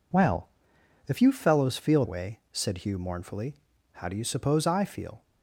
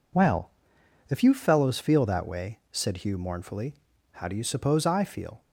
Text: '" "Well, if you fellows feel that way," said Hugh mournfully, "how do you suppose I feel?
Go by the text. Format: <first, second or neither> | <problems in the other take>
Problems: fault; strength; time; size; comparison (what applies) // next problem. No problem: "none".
second | skips "that"; at 2.0 s